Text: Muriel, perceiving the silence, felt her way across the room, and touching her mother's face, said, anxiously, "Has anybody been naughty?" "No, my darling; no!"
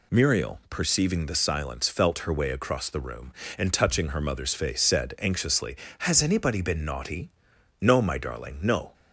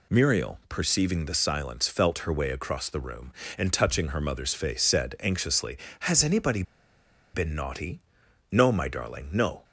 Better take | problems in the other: first | pauses between "anybody" and "been"; noticeable; at 6.6 s; 0.72 s long

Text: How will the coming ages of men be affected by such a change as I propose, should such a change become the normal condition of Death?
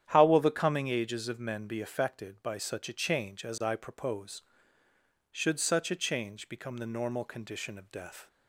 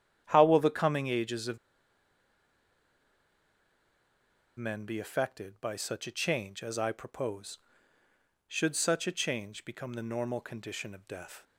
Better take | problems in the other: first | starts louder than the rest; strong; until 1.2 s; 9.5 dB; strong in the first // pauses between "of" and "men"; strong; at 1.5 s; 2.9 s long

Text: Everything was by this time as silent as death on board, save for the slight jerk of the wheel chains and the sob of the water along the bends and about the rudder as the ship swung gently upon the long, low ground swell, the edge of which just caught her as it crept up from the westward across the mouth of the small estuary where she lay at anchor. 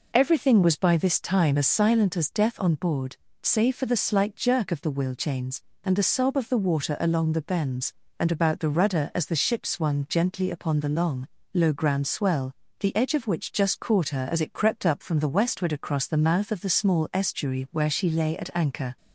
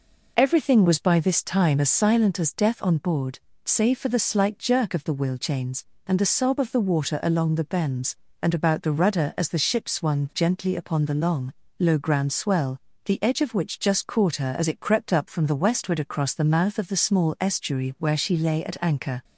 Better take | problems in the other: neither | none

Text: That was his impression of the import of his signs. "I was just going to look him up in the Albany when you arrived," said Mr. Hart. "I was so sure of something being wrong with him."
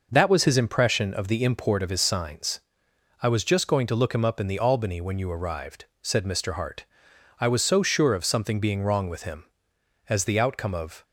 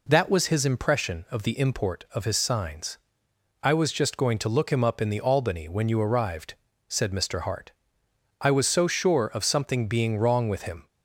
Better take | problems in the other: second | goes on to say "As the outcome of"; noticeable; from 10.0 s on; 0.96 s long

